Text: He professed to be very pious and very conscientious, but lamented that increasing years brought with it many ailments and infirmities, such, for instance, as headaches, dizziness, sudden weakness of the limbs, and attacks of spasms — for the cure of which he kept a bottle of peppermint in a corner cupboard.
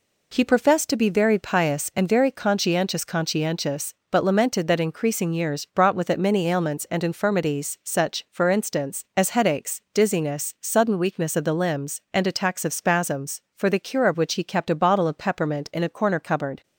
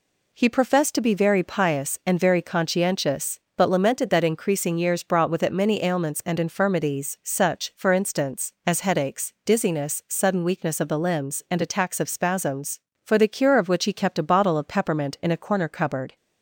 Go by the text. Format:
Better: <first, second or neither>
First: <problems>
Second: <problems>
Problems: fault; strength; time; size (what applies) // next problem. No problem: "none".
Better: second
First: says "conscientious" twice; at 3.0 s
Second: none